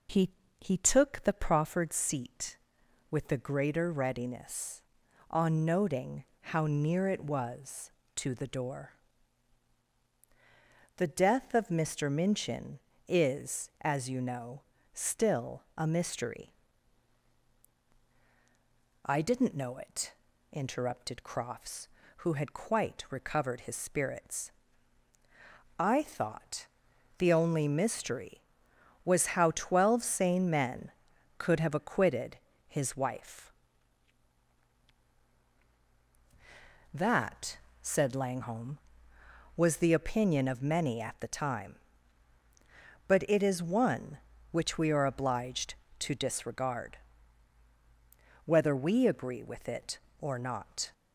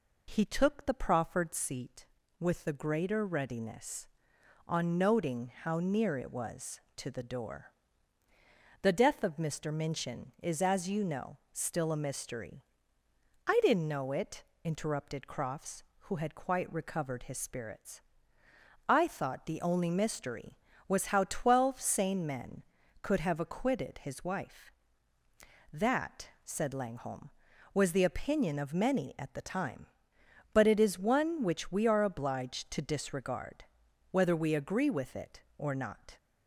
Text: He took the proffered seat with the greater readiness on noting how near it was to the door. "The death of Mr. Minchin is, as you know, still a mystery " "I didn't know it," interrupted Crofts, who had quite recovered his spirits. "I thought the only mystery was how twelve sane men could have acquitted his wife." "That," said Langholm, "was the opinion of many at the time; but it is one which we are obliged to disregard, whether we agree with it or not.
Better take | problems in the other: second | says "He" twice; at 0.5 s // pauses between "noting" and "how"; slight; at 6.2 s; 0.16 s long // pauses between "thought" and "the"; noticeable; at 26.6 s; 0.52 s long // pauses between "acquitted" and "his"; slight; at 32.3 s; 0.32 s long

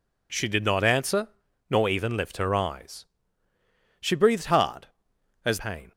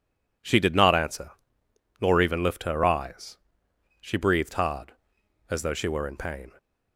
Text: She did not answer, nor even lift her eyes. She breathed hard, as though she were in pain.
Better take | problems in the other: second | skips "though she were in"; at 5.5 s

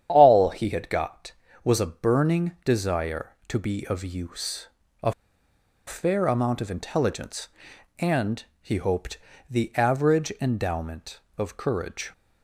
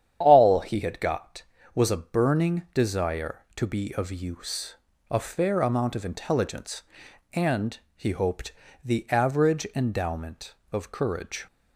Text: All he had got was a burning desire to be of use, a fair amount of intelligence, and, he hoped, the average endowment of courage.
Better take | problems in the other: second | starts louder than the rest; strong; until 1.1 s; 9.5 dB; strong in the second // pauses between "a" and "fair"; noticeable; at 5.1 s; 0.74 s long

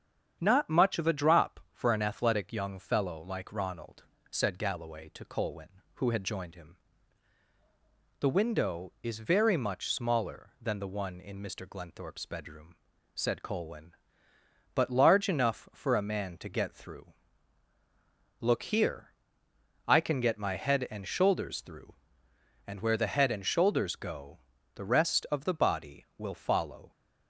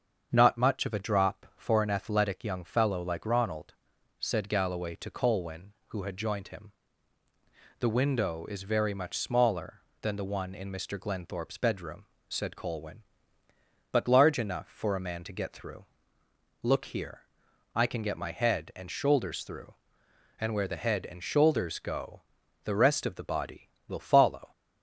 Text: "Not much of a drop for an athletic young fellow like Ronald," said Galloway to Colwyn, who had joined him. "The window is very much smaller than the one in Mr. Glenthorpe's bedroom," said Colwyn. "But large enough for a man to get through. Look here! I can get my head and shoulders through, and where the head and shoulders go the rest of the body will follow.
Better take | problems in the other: neither | starts louder than the rest; strong; the same in both // pauses between "go" and "the"; the same in both

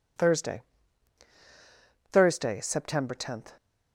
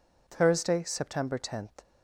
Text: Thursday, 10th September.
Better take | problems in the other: second | says "Thursday" twice; at 2.1 s

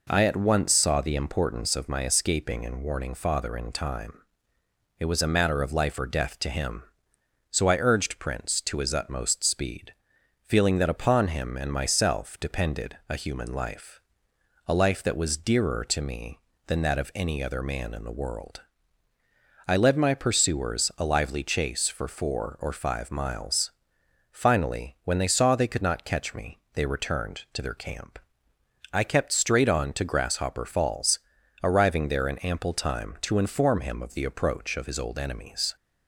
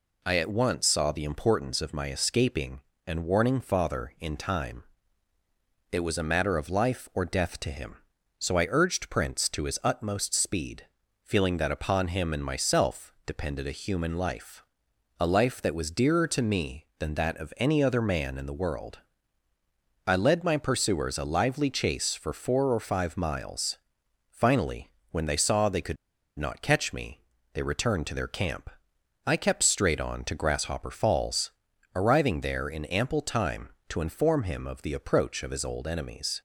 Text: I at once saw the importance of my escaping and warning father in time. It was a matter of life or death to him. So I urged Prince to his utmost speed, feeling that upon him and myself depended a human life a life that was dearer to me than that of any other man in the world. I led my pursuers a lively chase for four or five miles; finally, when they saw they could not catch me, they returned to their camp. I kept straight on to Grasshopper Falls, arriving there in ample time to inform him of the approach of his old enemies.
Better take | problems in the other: first | pauses between "life" and "a"; noticeable; at 14.6 s; 0.60 s long; noticeable in the first // pauses between "could" and "not"; at 25.9 s; 0.42 s long

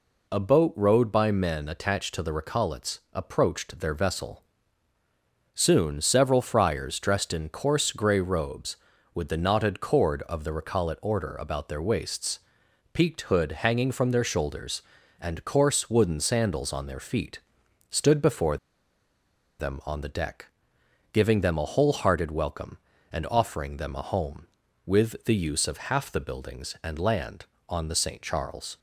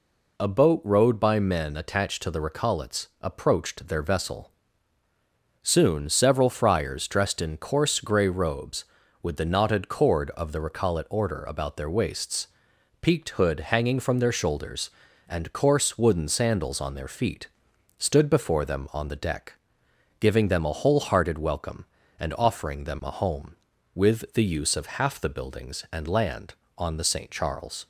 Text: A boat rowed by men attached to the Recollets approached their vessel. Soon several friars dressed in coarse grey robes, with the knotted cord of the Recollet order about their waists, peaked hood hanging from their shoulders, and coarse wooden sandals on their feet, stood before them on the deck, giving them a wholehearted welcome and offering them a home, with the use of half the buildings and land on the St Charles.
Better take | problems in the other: second | pauses between "Recollets" and "approached"; slight; at 2.9 s; 0.16 s long; slight in the second // pauses between "before" and "them"; at 18.5 s; 1.0 s long

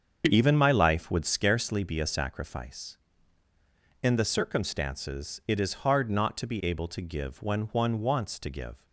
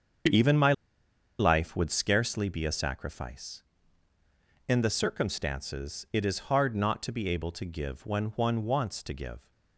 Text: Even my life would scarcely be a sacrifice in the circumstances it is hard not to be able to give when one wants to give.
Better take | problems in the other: first | starts louder than the rest; until 2.0 s; 7 dB; also in the first // pauses between "my" and "life"; noticeable; at 0.7 s; 0.66 s long

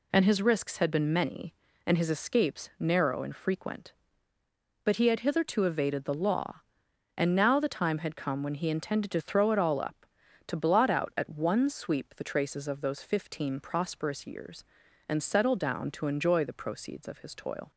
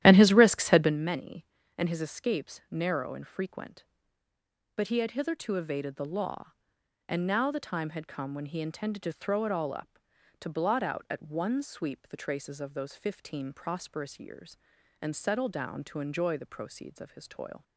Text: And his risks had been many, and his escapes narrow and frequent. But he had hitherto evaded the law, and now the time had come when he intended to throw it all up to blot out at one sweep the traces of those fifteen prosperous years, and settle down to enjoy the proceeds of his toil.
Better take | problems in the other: first | starts louder than the rest; strong; until 0.9 s; 12.5 dB

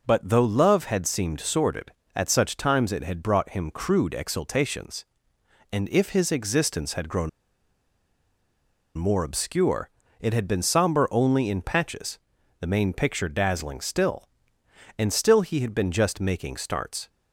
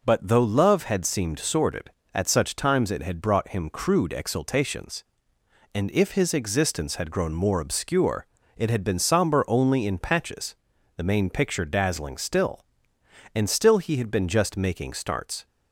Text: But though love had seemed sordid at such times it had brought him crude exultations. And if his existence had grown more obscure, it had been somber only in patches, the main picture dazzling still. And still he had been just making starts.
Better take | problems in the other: second | pauses between "grown" and "more"; strong; at 7.2 s; 1.6 s long

